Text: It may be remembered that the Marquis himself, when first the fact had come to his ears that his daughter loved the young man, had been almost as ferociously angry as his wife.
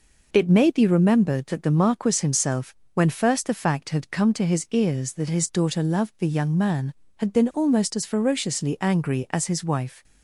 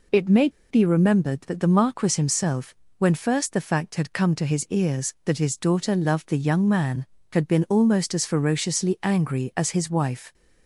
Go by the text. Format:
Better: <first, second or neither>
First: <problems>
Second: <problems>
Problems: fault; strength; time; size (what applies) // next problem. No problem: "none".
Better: first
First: none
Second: pauses between "may" and "be"; slight; at 0.4 s; 0.21 s long